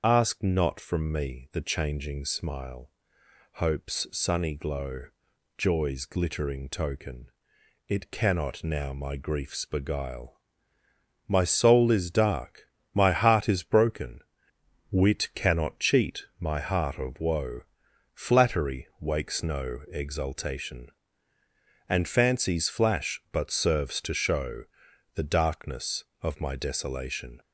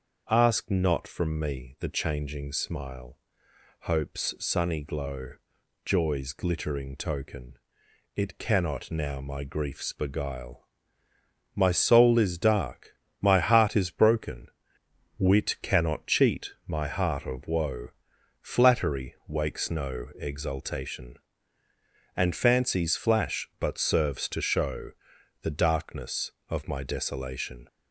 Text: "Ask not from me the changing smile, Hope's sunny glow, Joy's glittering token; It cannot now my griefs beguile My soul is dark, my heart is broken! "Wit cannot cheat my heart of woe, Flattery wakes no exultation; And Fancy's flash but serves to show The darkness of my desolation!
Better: second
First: loses the start of "Ask"; at 0.0 s; 40 ms // starts louder than the rest; until 1.0 s; 6.5 dB // pauses between "beguile" and "My"; noticeable; at 10.3 s; 0.90 s long // pauses between "show" and "The"; noticeable; at 24.6 s; 0.50 s long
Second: starts louder than the rest; until 1.2 s; 6.5 dB // pauses between "beguile" and "My"; noticeable; at 10.6 s; 0.90 s long // pauses between "show" and "The"; noticeable; at 24.9 s; 0.50 s long

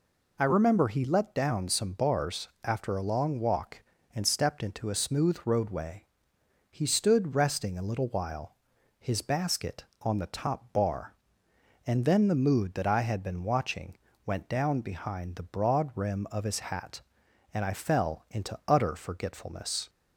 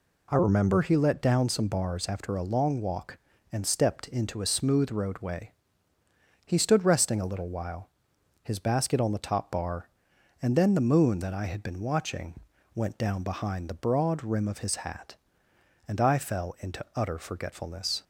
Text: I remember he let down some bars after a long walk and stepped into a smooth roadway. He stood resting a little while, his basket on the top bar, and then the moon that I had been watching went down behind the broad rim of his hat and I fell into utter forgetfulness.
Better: second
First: pauses between "bars" and "after"; slight; at 2.4 s; 0.16 s long // says "mood" for "moon"; at 12.3 s // pauses between "watching" and "went"; slight; at 13.9 s; 0.30 s long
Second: pauses between "watching" and "went"; slight; at 12.3 s; 0.36 s long

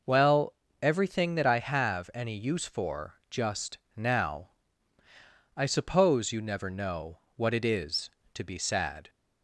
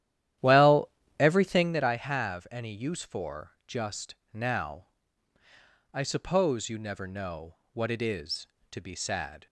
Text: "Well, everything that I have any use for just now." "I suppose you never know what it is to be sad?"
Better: first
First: pauses between "just" and "now"; slight; at 3.7 s; 0.18 s long // pauses between "know" and "what"; slight; at 7.1 s; 0.16 s long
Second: starts louder than the rest; strong; until 1.8 s; 11.5 dB // pauses between "just" and "now"; slight; at 4.1 s; 0.18 s long // pauses between "know" and "what"; slight; at 7.5 s; 0.16 s long

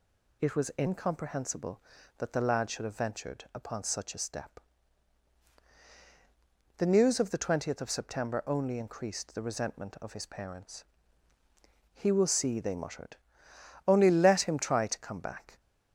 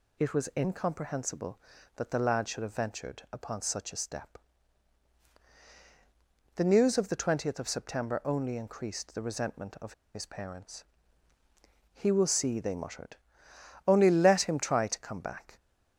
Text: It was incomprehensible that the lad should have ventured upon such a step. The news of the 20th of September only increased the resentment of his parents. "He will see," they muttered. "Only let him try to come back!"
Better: first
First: none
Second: pauses between "of" and "his"; slight; at 9.9 s; 0.20 s long

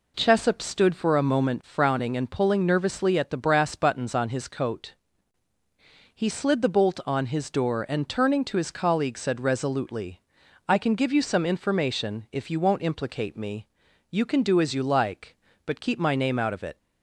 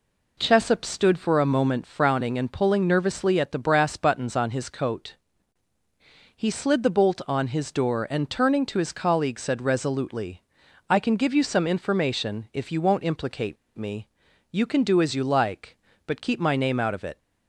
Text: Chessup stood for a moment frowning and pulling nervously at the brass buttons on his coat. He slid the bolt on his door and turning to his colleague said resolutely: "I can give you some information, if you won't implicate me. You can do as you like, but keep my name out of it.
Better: first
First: none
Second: pauses between "implicate" and "me"; slight; at 13.5 s; 0.21 s long

